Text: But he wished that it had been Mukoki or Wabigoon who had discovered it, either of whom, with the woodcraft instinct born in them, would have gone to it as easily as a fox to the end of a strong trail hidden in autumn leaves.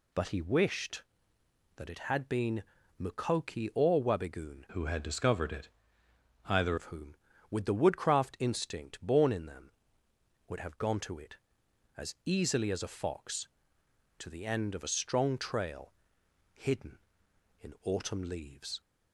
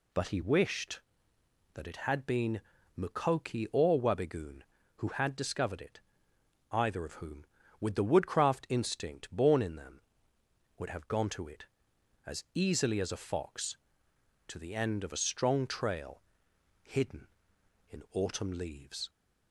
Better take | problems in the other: second | pauses between "been" and "Mukoki"; at 2.6 s; 0.38 s long; also in the second // changes voice from "who" to "either"; from 4.7 to 6.7 s; 2.0 s long // pauses between "trail" and "hidden"; noticeable; at 15.9 s; 0.62 s long; noticeable in the second

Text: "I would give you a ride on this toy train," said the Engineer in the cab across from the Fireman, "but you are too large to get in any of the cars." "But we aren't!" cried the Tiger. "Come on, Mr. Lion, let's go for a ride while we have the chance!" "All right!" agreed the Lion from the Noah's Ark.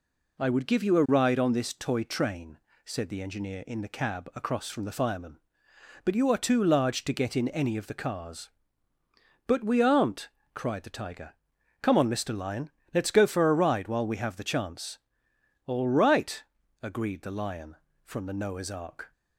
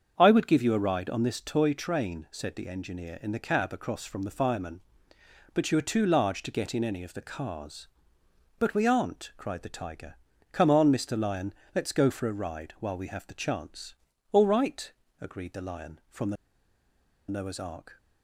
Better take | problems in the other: first | starts louder than the rest; until 1.1 s; 7 dB // pauses between "the" and "Noah's"; noticeable; at 16.3 s; 0.95 s long

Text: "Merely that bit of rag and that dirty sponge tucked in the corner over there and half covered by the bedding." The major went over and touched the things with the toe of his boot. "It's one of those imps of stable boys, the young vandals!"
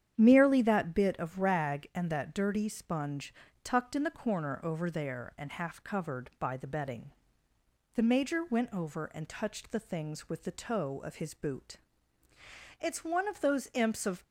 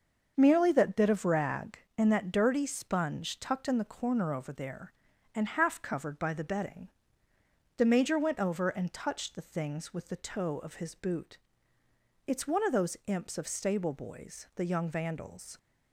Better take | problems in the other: second | starts louder than the rest; strong; until 1.1 s; 9 dB; also in the second // pauses between "sponge" and "tucked"; slight; at 3.3 s; 0.32 s long // stops before "stable boys the young vandals"; at 14.2 s

